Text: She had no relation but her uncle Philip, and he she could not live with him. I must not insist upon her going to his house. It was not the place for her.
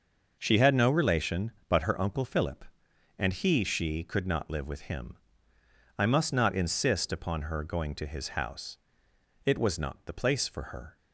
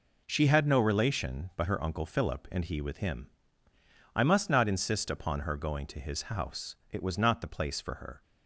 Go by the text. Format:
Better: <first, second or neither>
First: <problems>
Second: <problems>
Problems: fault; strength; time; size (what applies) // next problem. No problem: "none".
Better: first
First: none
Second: skips "she could not live"; at 2.8 s